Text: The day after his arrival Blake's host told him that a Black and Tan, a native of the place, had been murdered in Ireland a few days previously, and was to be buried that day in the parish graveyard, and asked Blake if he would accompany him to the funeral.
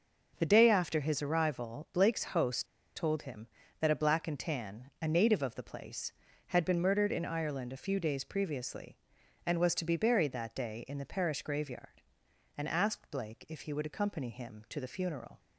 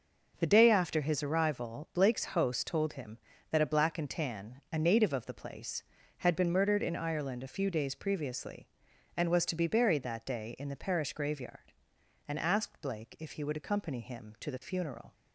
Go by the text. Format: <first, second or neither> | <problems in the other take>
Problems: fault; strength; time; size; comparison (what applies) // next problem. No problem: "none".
second | starts louder than the rest; until 1.3 s; 6.5 dB; noticeable in the second // pauses between "host" and "told"; slight; at 2.6 s; 0.30 s long